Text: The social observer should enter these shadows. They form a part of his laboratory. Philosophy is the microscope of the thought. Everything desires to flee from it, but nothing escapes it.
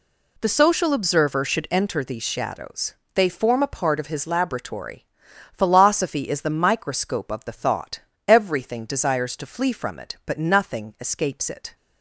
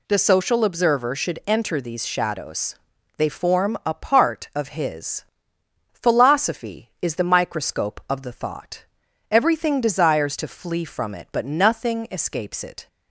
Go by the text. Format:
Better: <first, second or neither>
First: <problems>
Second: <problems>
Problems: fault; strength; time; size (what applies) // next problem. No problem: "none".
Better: first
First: none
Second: skips "laboratory"; at 5.5 s